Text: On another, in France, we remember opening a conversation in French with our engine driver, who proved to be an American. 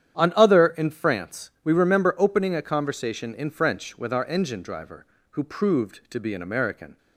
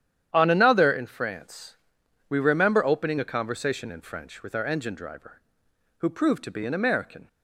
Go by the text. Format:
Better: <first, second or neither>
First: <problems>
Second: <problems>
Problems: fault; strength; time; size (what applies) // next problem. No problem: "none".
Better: second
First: starts louder than the rest; strong; until 1.2 s; 9.5 dB // says "other" for "another"; at 0.3 s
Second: starts louder than the rest; strong; until 1.3 s; 10 dB